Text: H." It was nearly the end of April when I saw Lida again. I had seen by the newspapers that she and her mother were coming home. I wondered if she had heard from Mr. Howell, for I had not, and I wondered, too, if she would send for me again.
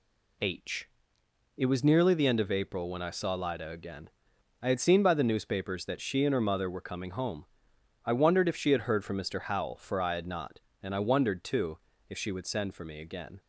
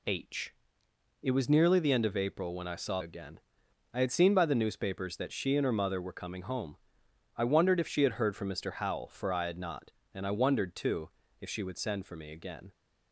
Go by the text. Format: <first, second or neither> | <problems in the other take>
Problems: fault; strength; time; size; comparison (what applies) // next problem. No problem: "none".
first | skips "Lida"; at 3.0 s